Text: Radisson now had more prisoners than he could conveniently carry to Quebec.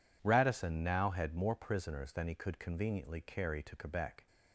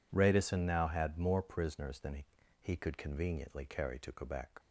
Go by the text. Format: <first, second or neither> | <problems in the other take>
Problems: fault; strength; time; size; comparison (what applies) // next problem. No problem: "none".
first | says "he" twice; at 2.6 s